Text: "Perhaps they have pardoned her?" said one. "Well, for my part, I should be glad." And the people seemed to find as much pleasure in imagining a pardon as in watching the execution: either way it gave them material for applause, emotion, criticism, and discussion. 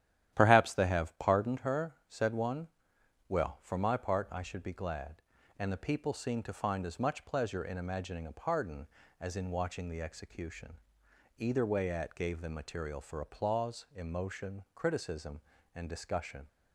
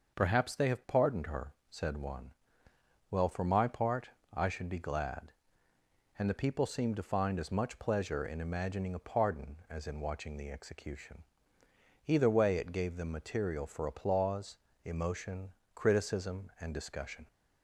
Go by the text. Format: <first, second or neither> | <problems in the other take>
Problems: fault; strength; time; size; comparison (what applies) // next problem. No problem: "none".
second | starts louder than the rest; strong; until 1.3 s; 12 dB; noticeable in the second // says "at" for "it"; at 11.9 s